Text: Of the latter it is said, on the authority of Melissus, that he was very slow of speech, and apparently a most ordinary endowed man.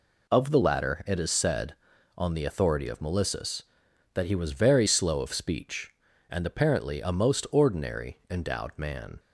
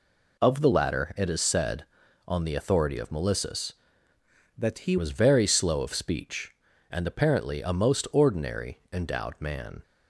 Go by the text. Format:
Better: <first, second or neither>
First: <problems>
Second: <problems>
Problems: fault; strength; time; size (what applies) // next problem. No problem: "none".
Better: first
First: none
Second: changes voice from "that" to "he"; from 4.5 to 4.9 s; 0.4 s long